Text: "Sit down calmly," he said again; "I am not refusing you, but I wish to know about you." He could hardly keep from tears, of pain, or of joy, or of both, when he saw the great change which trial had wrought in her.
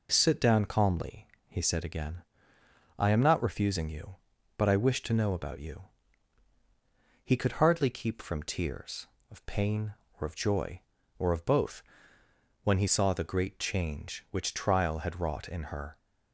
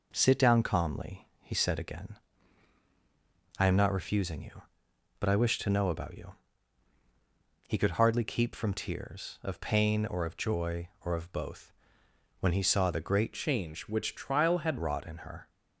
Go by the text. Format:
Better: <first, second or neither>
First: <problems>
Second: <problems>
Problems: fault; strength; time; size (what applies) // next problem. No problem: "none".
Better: first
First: none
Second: changes voice from "change" to "had"; from 13.3 to 14.7 s; 1.4 s long